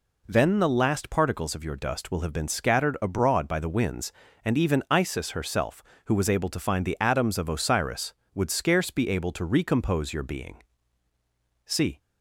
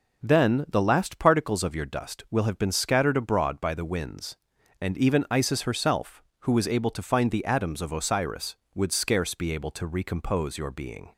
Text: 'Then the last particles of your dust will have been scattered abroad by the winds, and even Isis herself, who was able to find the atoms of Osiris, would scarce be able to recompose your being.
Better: second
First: goes on to say "See"; slight; from 11.6 s on; 0.34 s long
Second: none

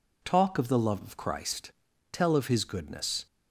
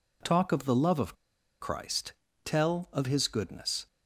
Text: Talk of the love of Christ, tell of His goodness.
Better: first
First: none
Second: pauses between "of" and "Christ"; at 1.1 s; 0.45 s long

